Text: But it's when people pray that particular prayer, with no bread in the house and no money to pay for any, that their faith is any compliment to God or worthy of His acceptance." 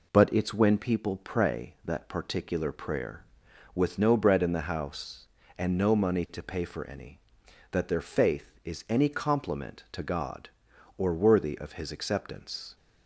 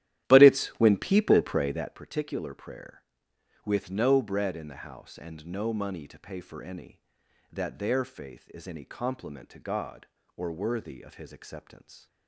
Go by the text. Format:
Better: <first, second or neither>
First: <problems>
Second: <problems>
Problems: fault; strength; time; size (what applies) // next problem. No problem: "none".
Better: first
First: none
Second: starts louder than the rest; strong; until 2.0 s; 13 dB